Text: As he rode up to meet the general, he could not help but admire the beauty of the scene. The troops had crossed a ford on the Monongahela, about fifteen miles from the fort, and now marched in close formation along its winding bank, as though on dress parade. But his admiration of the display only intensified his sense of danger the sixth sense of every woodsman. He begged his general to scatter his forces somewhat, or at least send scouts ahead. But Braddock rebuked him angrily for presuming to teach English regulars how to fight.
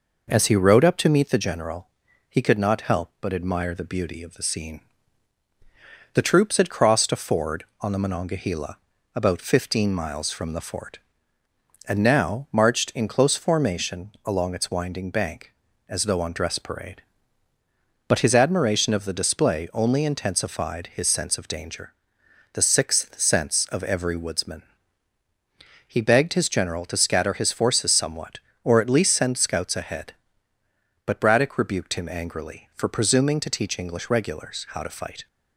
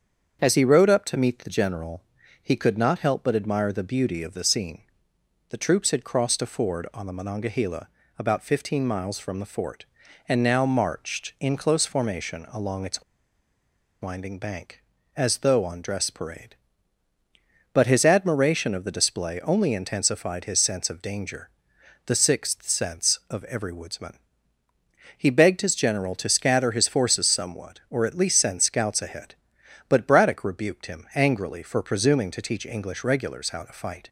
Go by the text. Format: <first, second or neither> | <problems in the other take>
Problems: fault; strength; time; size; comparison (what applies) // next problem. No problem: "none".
first | starts louder than the rest; strong; until 1.4 s; 7.5 dB // pauses between "its" and "winding"; at 13.0 s; 0.99 s long // pauses between "danger" and "the"; noticeable; at 21.5 s; 0.56 s long; noticeable in the first